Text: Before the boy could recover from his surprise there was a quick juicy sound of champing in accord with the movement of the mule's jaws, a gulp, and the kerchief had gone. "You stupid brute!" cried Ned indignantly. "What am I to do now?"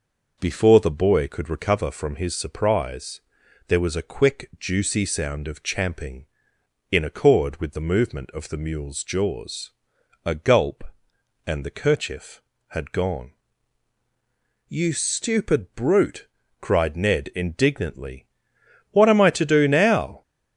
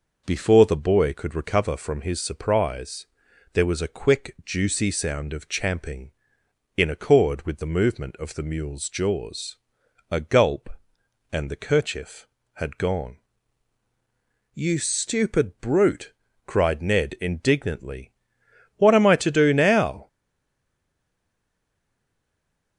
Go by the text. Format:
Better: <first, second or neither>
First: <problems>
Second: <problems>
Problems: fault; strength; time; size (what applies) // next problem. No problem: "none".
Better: first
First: pauses between "surprise" and "there"; noticeable; at 3.1 s; 0.46 s long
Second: pauses between "surprise" and "there"; noticeable; at 3.0 s; 0.46 s long // stays silent after the last word; strong; from 20.0 s on; 2.7 s long